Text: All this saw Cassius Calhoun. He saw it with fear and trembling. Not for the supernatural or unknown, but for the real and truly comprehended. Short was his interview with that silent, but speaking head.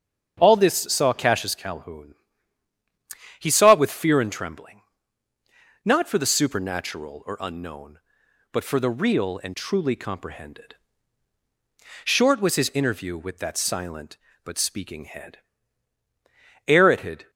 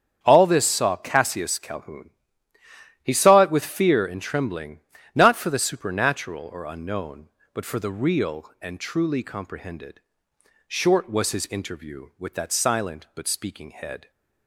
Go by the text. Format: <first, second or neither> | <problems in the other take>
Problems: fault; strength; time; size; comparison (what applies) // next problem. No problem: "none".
second | starts louder than the rest; strong; until 1.3 s; 7.5 dB; strong in the second // goes on to say "Ere it had"; noticeable; from 16.6 s on; 0.64 s long